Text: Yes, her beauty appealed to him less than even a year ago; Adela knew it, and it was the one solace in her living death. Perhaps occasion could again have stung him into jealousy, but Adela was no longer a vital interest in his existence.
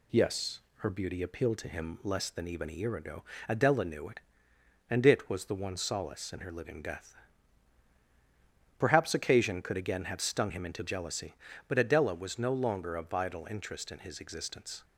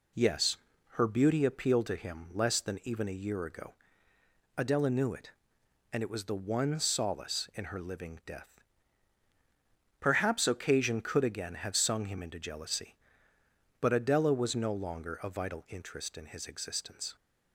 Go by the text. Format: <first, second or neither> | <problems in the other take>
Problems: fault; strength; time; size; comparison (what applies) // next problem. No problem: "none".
first | says "sung" for "stung"; at 11.7 s